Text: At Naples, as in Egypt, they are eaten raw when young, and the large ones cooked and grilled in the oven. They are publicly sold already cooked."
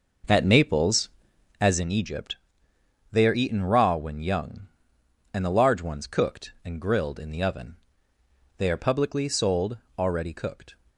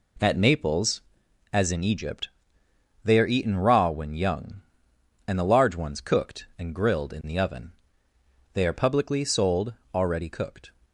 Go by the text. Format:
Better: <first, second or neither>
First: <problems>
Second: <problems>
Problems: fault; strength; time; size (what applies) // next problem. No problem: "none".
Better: second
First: starts louder than the rest; noticeable; until 1.8 s; 6 dB // pauses between "sold" and "already"; slight; at 9.7 s; 0.18 s long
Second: pauses between "sold" and "already"; slight; at 9.7 s; 0.18 s long